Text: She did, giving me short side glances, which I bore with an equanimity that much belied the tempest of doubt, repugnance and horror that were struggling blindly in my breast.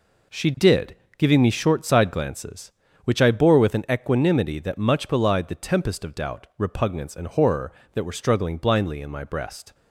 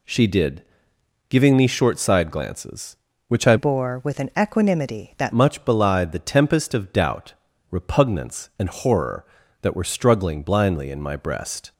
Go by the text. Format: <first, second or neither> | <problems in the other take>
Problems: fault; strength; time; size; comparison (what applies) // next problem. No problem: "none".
first | changes voice from "bore" to "that"; from 3.5 to 5.3 s; 1.8 s long